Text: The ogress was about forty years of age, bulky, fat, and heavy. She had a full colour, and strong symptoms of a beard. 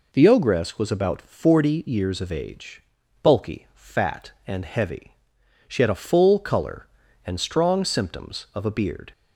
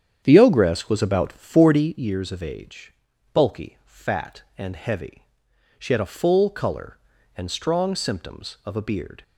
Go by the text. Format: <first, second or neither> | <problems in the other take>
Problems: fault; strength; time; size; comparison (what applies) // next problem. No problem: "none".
first | starts louder than the rest; strong; until 2.0 s; 8.5 dB